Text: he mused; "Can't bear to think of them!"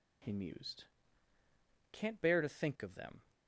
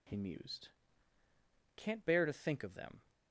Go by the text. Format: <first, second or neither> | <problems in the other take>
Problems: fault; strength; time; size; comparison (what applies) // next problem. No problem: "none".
neither | none